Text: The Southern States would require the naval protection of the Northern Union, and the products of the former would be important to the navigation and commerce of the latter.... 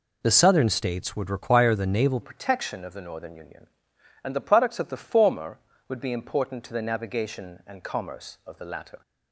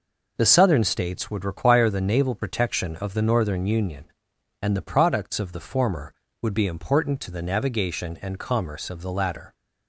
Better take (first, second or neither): second